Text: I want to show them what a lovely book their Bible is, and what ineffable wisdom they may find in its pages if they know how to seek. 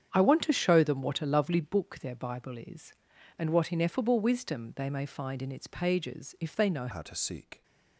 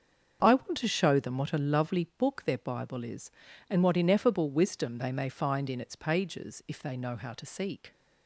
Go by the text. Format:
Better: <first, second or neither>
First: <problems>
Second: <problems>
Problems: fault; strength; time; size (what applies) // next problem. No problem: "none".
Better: second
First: starts louder than the rest; strong; until 1.1 s; 8 dB // changes voice at "how"; from 6.9 s on; 0.7 s long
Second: starts louder than the rest; until 1.4 s; 7 dB